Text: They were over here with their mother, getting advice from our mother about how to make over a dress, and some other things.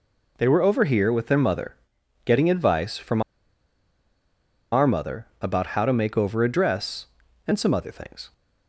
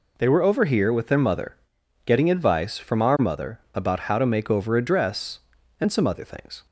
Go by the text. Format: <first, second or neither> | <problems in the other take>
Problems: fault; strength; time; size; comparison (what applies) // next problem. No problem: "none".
second | pauses between "from" and "our"; strong; at 3.2 s; 1.5 s long